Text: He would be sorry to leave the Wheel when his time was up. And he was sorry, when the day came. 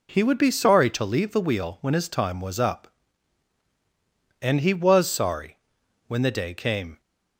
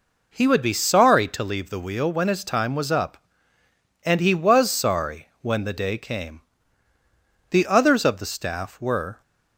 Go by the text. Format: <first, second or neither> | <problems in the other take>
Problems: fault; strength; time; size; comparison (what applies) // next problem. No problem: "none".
first | goes on to say "The others of the staff were"; strong; from 7.4 s on; 1.7 s long